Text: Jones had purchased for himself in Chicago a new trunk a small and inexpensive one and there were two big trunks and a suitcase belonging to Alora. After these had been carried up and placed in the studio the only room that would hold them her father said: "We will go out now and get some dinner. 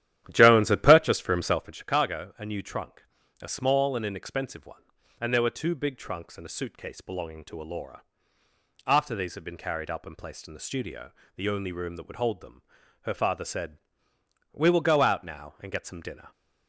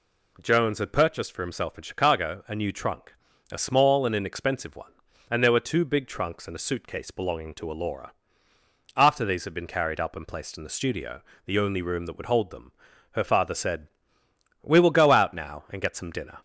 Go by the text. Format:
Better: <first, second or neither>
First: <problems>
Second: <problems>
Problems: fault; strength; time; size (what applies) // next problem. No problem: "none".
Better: second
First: starts louder than the rest; strong; until 1.8 s; 12 dB // pauses between "trunk" and "a"; at 3.0 s; 0.38 s long // pauses between "studio" and "the"; slight; at 11.1 s; 0.24 s long // pauses between "them" and "her"; at 12.6 s; 0.40 s long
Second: pauses between "trunk" and "a"; at 3.1 s; 0.38 s long // pauses between "studio" and "the"; slight; at 11.2 s; 0.24 s long // pauses between "them" and "her"; at 12.7 s; 0.40 s long